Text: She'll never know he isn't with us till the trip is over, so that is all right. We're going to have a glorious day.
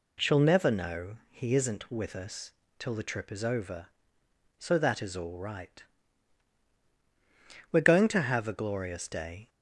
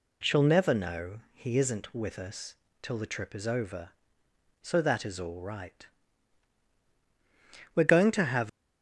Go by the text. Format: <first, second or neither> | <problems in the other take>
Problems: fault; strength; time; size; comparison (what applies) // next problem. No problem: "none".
first | pauses between "know" and "he"; slight; at 1.1 s; 0.16 s long; slight in the first // pauses between "us" and "till"; slight; at 2.5 s; 0.26 s long; slight in the first // stops before "a glorious day"; at 8.4 s